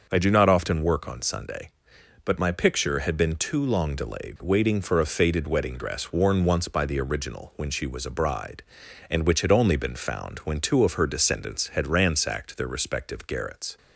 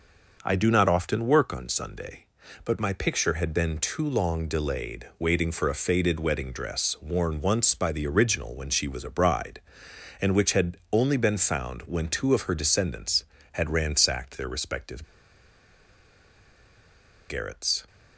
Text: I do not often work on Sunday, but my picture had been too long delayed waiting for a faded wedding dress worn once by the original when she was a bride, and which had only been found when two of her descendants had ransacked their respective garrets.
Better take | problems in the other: first | starts louder than the rest; noticeable; until 1.4 s; 6 dB; noticeable in the first // pauses between "had" and "only"; slight; at 10.7 s; 0.16 s long // pauses between "respective" and "garrets"; strong; at 15.0 s; 2.2 s long

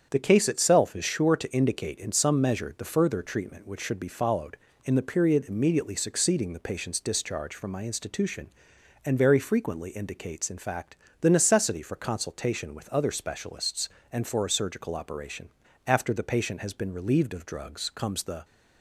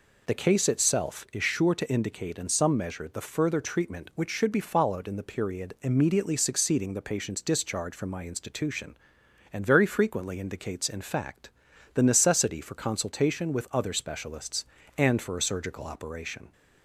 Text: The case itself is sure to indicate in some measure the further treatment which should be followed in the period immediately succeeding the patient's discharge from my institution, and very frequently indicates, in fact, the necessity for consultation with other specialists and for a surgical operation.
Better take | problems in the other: second | starts louder than the rest; strong; until 1.1 s; 8 dB // goes on to say "After the patient has been relieved of drugs comes the"; strong; from 15.8 s on; 2.5 s long

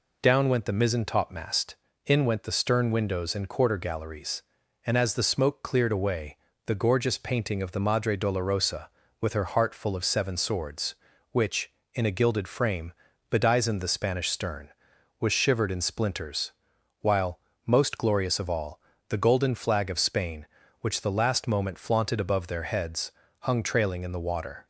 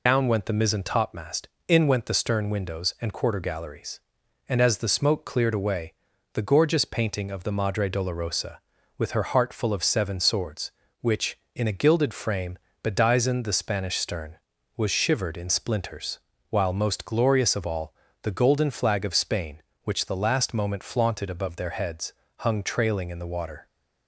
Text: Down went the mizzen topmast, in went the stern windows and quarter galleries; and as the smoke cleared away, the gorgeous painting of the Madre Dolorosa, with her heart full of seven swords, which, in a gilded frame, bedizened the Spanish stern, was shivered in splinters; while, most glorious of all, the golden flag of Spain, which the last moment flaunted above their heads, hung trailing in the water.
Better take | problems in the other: first | loses the start of "Down"; at 0.0 s; 75 ms

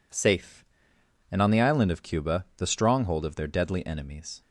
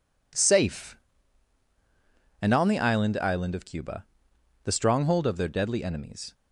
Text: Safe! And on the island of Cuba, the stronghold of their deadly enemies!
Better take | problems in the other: first | says "island" twice; at 3.1 s

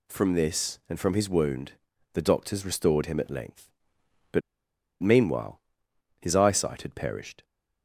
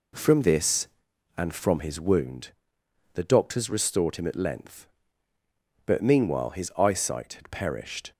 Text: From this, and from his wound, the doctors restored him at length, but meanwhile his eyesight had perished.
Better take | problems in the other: second | pauses between "but" and "meanwhile"; noticeable; at 4.4 s; 0.60 s long // pauses between "meanwhile" and "his"; noticeable; at 5.6 s; 0.58 s long

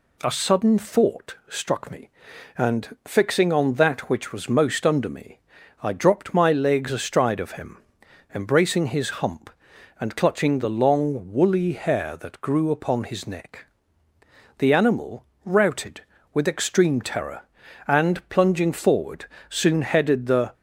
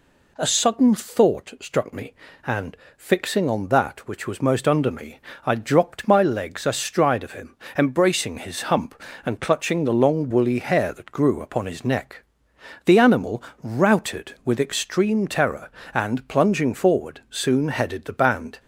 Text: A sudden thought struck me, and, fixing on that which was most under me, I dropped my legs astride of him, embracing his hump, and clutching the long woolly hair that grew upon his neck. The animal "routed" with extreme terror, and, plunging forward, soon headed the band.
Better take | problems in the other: second | pauses between "animal" and "routed"; slight; at 15.2 s; 0.18 s long; slight in the second // stops before "band"; at 20.5 s

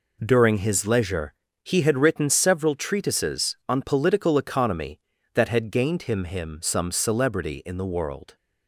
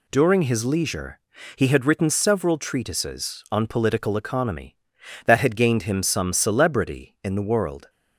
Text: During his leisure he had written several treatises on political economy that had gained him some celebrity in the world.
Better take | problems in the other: second | pauses between "leisure" and "he"; slight; at 1.3 s; 0.30 s long; slight in the second // says "him" twice; at 6.2 s

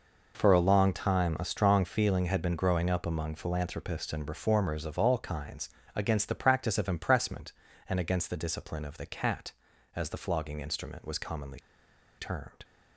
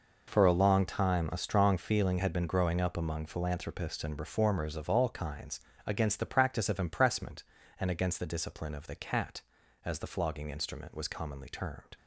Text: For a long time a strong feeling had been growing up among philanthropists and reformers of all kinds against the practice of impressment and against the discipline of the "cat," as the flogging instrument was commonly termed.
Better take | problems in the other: second | pauses between "kinds" and "against"; slight; at 5.6 s; 0.26 s long; slight in the second // pauses between "commonly" and "termed"; noticeable; at 11.5 s; 0.60 s long

